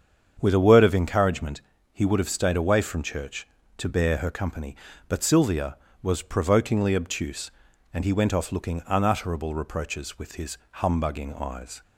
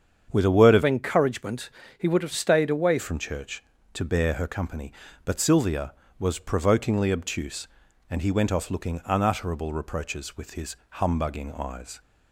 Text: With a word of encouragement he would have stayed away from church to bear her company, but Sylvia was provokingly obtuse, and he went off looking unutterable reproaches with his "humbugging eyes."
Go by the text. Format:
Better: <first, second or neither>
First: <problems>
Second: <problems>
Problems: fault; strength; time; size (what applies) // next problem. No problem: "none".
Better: first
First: starts louder than the rest; strong; until 1.4 s; 7.5 dB // pauses between "encouragement" and "he"; slight; at 1.6 s; 0.32 s long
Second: starts louder than the rest; strong; until 1.3 s; 7.5 dB // changes voice from "encouragement" to "away"; from 0.8 to 2.9 s; 2.1 s long // pauses between "encouragement" and "he"; slight; at 1.6 s; 0.28 s long